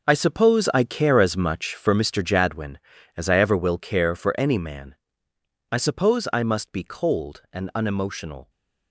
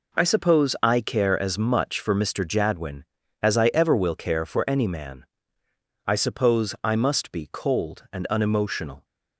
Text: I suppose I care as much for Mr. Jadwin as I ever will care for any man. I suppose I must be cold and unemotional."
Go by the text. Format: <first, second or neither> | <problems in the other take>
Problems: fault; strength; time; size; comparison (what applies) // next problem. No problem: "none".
second | gets quieter; strong; throughout; 11 dB